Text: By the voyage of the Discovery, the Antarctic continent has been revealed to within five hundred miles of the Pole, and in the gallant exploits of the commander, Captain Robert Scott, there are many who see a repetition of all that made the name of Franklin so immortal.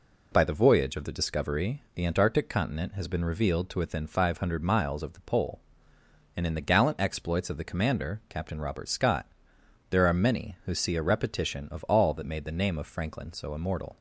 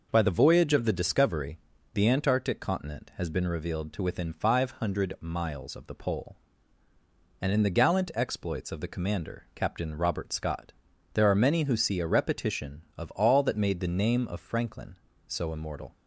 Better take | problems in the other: neither | none

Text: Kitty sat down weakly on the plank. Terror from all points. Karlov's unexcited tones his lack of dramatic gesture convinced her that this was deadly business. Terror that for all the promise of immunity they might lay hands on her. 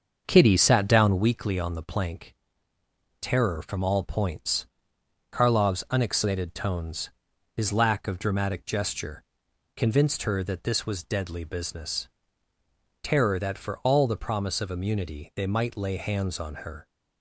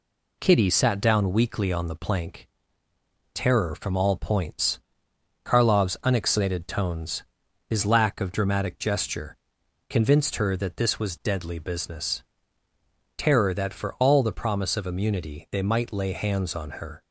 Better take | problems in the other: second | starts louder than the rest; until 1.4 s; 6.5 dB // pauses between "tones" and "his"; noticeable; at 7.0 s; 0.46 s long; noticeable in the second // pauses between "gesture" and "convinced"; noticeable; at 9.2 s; 0.52 s long; noticeable in the second

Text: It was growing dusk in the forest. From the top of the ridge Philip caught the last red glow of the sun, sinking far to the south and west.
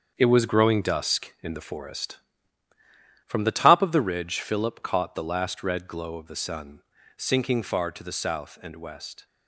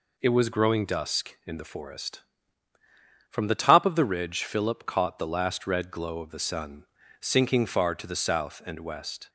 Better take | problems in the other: second | gets quieter; strong; throughout; 8 dB

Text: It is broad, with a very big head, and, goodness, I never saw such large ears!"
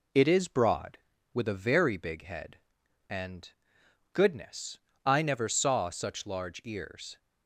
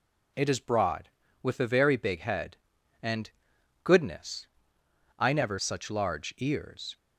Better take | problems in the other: first | skips "saw"; at 5.5 s

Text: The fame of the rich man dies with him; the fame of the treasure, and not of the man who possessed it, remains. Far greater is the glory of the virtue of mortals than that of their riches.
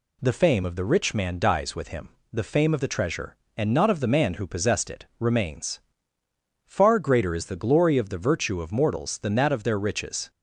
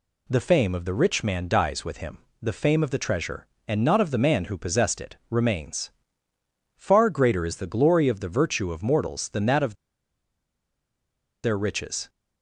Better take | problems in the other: first | pauses between "of" and "their"; strong; at 9.7 s; 1.6 s long

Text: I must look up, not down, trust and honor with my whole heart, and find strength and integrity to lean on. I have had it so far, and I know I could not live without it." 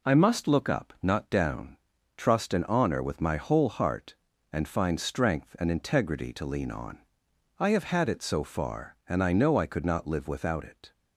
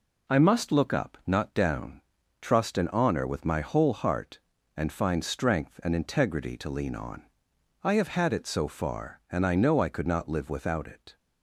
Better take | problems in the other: neither | none

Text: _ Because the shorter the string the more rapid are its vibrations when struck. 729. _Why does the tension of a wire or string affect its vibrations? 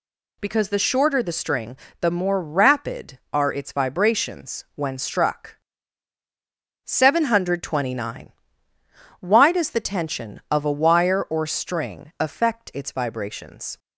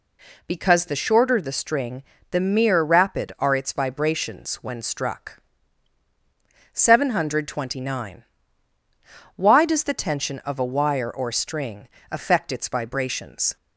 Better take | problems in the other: first | pauses between "string" and "the"; slight; at 2.0 s; 0.28 s long; slight in the first // says "mere" for "more"; at 2.3 s // pauses between "string" and "affect"; slight; at 11.8 s; 0.22 s long

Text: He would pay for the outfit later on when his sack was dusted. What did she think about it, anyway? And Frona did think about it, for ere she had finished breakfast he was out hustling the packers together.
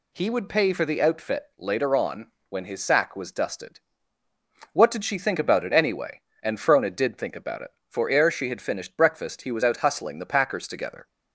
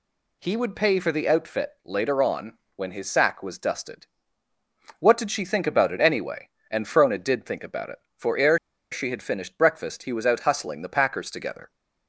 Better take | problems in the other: first | pauses between "on" and "when"; slight; at 2.5 s; 0.20 s long; slight in the first // pauses between "ere" and "she"; slight; at 8.5 s; 0.33 s long

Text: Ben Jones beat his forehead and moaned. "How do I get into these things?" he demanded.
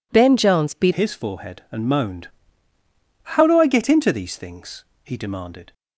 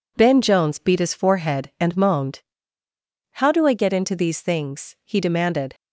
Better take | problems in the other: second | changes voice at "his"; from 0.9 s on; 4.8 s long

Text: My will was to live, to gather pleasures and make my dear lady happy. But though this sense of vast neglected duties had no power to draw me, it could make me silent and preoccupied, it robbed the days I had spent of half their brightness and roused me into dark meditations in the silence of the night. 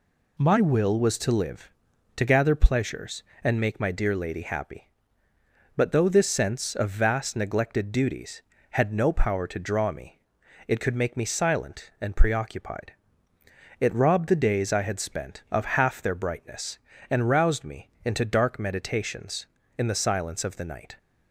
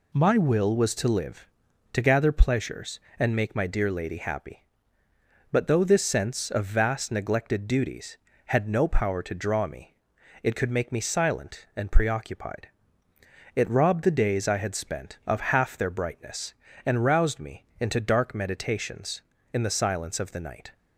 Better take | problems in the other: neither | none

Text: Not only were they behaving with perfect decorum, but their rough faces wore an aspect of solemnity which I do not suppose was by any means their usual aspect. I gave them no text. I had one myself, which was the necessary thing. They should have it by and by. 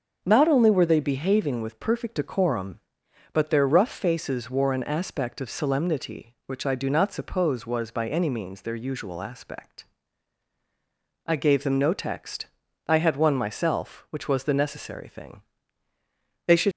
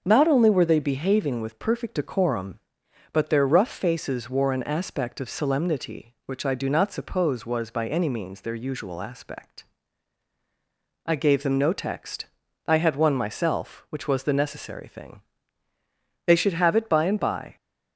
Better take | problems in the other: second | starts louder than the rest; until 1.2 s; 6.5 dB; also in the second // stops before "have it by and by"; at 16.7 s

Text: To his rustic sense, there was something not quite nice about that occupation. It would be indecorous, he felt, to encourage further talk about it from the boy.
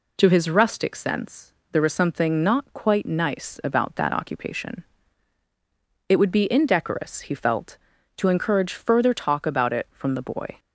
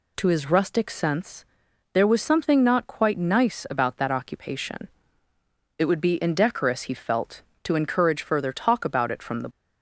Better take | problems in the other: first | stops before "boy"; at 9.5 s

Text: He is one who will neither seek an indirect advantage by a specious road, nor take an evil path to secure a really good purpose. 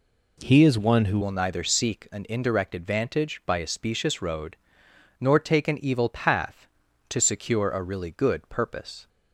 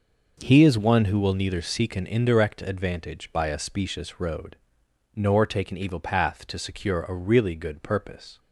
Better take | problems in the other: second | changes voice at "will"; from 1.2 s on; 7.8 s long

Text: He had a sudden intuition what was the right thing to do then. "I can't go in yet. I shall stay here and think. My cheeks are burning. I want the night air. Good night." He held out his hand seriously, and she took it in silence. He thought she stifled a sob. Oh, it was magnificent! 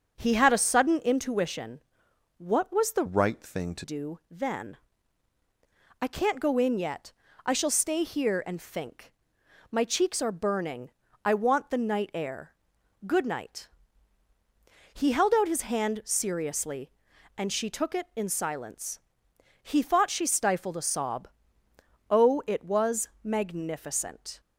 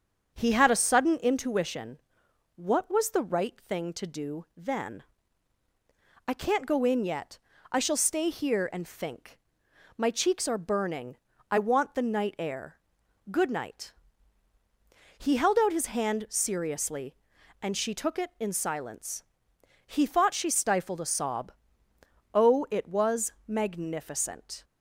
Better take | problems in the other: second | starts louder than the rest; until 1.1 s; 7 dB; strong in the second // pauses between "intuition" and "what"; noticeable; at 1.8 s; 0.58 s long; noticeable in the second // changes voice from "right" to "to"; from 3.0 to 3.8 s; 0.8 s long // pauses between "was" and "magnificent"; slight; at 23.0 s; 0.16 s long; slight in the second

